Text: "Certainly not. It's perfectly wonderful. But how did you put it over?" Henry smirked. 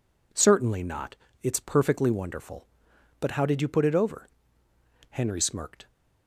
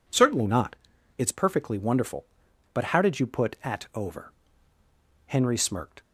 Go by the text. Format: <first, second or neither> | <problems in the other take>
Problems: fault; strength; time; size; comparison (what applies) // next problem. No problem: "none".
first | says "at" for "it"; at 3.6 s